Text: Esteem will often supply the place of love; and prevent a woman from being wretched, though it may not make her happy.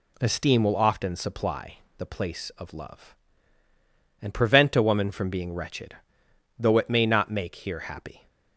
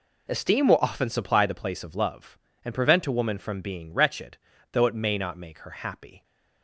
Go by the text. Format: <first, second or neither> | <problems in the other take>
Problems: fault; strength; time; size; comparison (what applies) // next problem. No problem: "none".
second | pauses between "supply" and "the"; slight; at 1.7 s; 0.18 s long // says "here" for "her"; at 7.5 s